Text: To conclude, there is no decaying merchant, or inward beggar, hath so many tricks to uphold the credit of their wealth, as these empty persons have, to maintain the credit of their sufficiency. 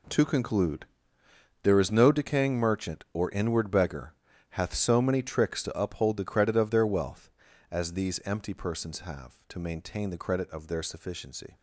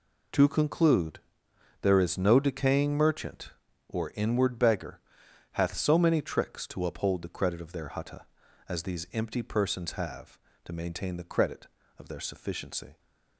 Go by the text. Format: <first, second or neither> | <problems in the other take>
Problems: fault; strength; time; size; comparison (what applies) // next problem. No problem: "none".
first | says "hutta" for "wealth"; at 7.8 s